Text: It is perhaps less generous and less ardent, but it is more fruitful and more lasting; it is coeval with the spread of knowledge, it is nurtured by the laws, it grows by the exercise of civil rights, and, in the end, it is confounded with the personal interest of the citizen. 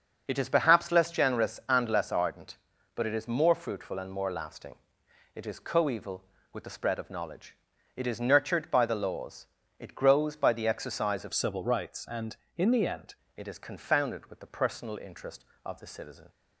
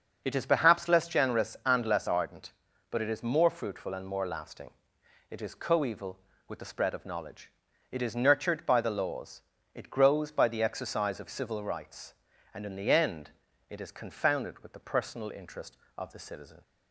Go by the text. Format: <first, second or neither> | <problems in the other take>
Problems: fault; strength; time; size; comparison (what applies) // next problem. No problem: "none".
second | starts louder than the rest; until 1.2 s; 6.5 dB; also in the second // changes voice from "civil" to "end"; from 11.3 to 13.1 s; 1.8 s long